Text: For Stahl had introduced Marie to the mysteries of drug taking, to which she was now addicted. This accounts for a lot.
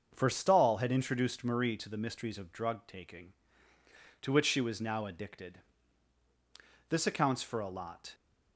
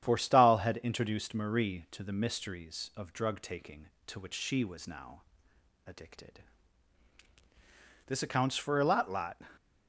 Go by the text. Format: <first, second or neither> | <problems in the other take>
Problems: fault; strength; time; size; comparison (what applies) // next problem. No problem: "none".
first | starts louder than the rest; strong; until 1.0 s; 9 dB; also in the first // pauses between "now" and "addicted"; noticeable; at 5.2 s; 0.66 s long // says "lot" twice; at 9.0 s